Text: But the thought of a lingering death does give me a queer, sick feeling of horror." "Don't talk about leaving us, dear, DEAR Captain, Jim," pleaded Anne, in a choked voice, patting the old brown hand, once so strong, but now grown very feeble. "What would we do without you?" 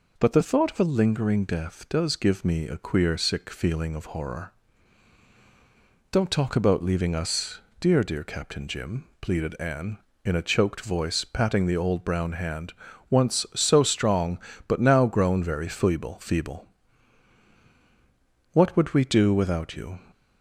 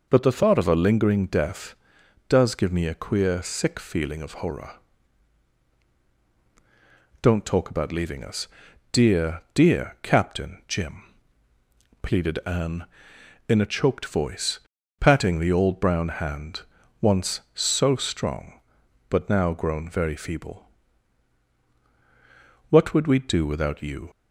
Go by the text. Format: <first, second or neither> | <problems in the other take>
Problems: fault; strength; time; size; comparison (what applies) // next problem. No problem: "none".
second | says "feeble" twice; at 16.1 s